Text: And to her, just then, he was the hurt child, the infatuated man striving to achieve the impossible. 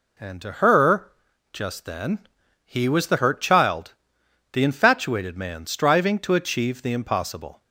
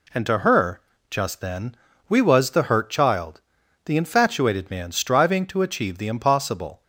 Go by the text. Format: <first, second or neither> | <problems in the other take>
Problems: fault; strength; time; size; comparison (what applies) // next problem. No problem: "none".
first | says "we" for "he"; at 2.0 s